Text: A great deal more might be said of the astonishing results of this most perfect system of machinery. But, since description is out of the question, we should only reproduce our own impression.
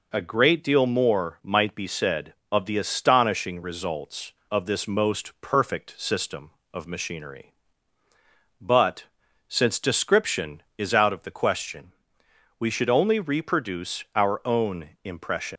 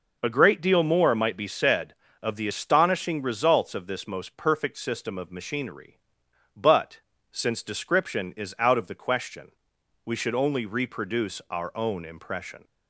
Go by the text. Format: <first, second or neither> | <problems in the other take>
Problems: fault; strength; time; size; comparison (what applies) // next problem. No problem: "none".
second | pauses between "own" and "impression"; slight; at 14.8 s; 0.16 s long // leaves "impression" unfinished; at 15.5 s; 130 ms